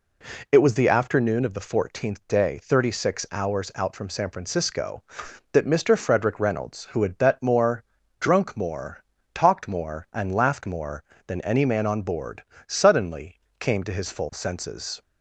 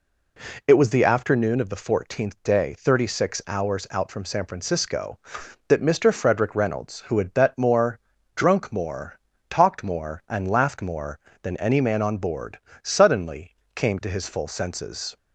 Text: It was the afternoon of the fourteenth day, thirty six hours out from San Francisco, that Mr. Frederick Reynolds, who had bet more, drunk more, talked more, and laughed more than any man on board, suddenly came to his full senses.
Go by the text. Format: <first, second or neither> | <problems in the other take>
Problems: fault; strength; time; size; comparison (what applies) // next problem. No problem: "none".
neither | pauses between "suddenly" and "came"; slight; the same in both